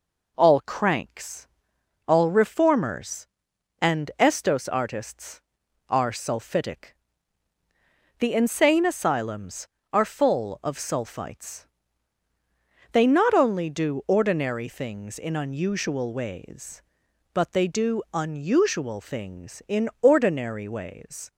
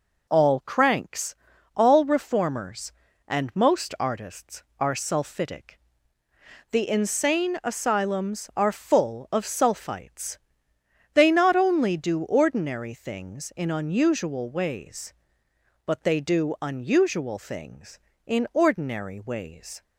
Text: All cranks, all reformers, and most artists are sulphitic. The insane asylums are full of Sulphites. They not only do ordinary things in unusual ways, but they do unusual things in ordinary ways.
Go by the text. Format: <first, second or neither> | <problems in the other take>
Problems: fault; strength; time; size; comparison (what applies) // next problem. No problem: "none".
second | says "estos" for "most"; at 4.1 s